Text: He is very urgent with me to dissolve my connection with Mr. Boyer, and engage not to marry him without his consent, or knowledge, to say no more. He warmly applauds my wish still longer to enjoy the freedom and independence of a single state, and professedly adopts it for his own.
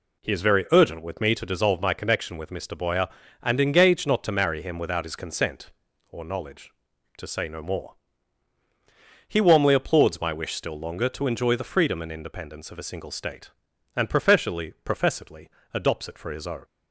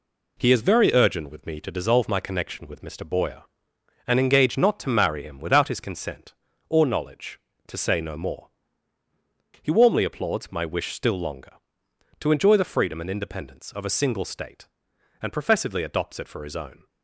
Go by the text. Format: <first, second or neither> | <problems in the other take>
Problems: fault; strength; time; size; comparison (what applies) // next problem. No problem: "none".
second | says "professedly" twice; at 14.8 s